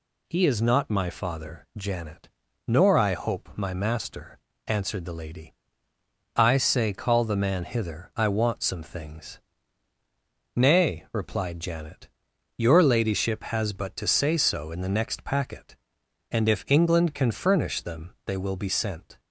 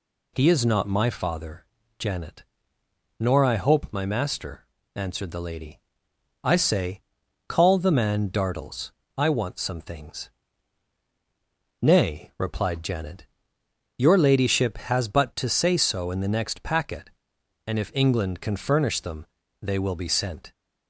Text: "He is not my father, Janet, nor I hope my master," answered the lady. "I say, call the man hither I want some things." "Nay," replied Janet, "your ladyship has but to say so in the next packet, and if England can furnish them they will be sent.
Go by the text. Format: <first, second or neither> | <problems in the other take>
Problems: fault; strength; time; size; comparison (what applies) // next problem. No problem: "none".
first | says "dartles" for "hither"; at 8.2 s // pauses between "them" and "they"; slight; at 19.2 s; 0.34 s long